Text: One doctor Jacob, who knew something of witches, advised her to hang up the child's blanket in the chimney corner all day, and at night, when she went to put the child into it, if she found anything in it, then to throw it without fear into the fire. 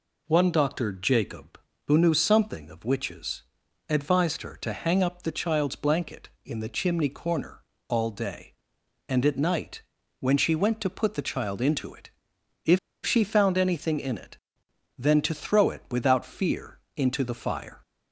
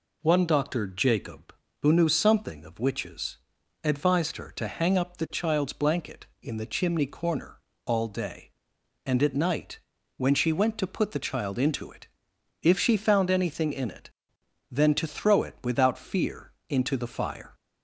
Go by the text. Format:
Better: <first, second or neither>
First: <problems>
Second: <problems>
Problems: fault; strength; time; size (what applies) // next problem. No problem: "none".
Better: second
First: pauses between "corner" and "all"; slight; at 7.6 s; 0.28 s long // pauses between "if" and "she"; slight; at 12.7 s; 0.26 s long // pauses between "fear" and "into"; slight; at 16.7 s; 0.16 s long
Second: pauses between "corner" and "all"; slight; at 7.5 s; 0.28 s long // pauses between "fear" and "into"; slight; at 16.5 s; 0.16 s long